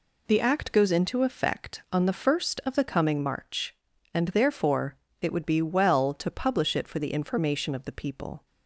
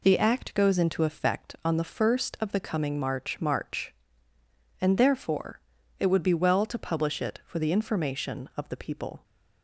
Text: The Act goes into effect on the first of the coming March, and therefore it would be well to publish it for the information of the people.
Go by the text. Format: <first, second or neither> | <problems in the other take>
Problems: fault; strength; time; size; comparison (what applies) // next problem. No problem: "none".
first | says "March" twice; at 3.3 s // pauses between "therefore" and "it"; slight; at 5.6 s; 0.36 s long; slight in the first